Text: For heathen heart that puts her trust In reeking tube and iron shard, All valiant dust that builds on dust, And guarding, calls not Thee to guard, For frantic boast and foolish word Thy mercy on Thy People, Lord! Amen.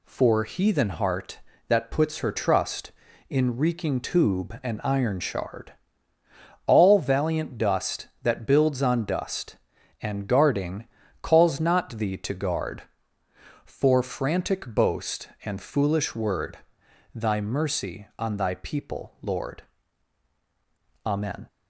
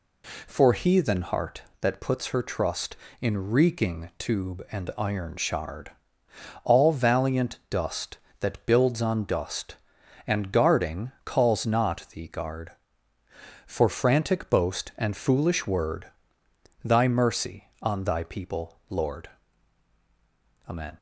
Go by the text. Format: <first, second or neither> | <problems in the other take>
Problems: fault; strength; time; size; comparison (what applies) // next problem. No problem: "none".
first | skips "to"; at 12.2 s // pauses between "word" and "Thy"; noticeable; at 16.0 s; 0.76 s long; noticeable in the first